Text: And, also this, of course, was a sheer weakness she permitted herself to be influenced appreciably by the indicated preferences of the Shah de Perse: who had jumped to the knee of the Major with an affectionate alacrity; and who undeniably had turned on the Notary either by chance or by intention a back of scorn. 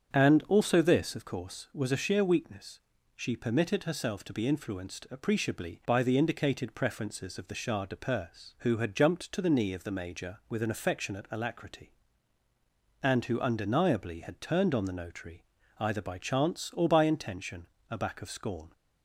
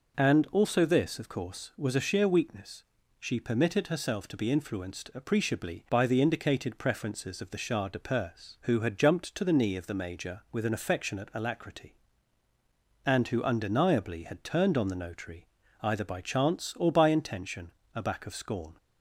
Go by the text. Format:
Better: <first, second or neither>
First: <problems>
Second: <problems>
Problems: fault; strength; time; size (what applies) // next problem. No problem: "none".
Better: second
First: starts louder than the rest; strong; until 1.2 s; 8 dB // pauses between "weakness" and "she"; slight; at 2.7 s; 0.36 s long // pauses between "Notary" and "either"; slight; at 15.4 s; 0.34 s long // pauses between "intention" and "a"; slight; at 17.6 s; 0.24 s long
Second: pauses between "weakness" and "she"; slight; at 2.8 s; 0.36 s long // pauses between "Notary" and "either"; slight; at 15.4 s; 0.34 s long // pauses between "intention" and "a"; slight; at 17.7 s; 0.24 s long